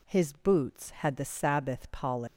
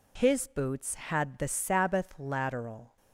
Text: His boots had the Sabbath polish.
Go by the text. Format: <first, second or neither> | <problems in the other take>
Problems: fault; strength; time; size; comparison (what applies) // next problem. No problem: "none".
first | says "lateral" for "polish"; at 2.1 s